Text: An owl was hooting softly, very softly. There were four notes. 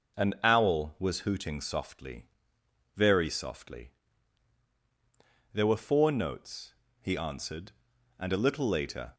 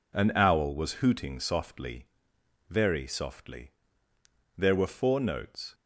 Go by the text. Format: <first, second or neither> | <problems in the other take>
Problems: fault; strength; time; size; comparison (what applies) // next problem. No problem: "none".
second | goes on to say "He answered and a little later"; strong; from 7.0 s on; 2.1 s long